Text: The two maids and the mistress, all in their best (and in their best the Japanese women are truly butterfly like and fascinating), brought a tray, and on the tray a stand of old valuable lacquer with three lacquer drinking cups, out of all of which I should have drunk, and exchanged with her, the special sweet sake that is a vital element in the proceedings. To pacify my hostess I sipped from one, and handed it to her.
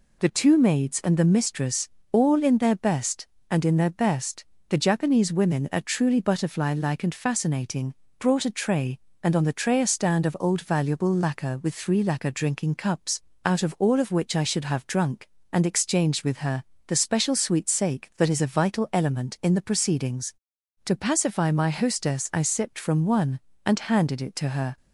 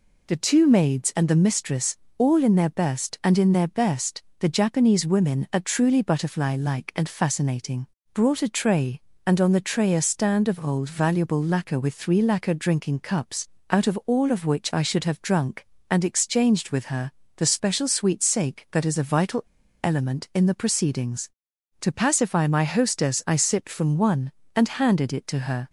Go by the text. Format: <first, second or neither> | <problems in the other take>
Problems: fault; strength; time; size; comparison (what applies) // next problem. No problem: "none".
first | pauses between "best" and "the"; slight; at 4.2 s; 0.18 s long; slight in the first // pauses between "vital" and "element"; at 19.4 s; 0.39 s long